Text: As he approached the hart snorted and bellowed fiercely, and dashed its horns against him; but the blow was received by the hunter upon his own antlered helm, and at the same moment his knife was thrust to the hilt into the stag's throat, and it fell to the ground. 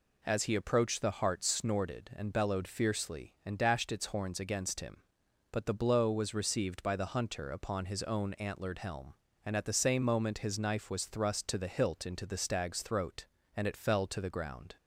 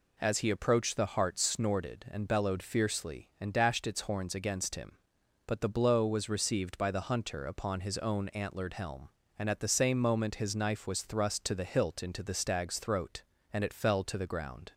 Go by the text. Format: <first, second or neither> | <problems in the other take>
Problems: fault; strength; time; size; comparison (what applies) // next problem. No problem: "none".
neither | none